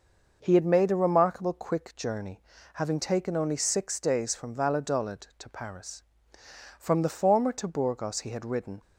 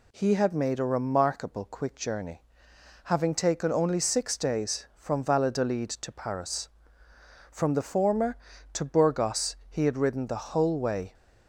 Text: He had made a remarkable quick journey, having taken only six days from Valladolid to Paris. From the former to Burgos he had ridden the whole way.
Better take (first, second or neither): second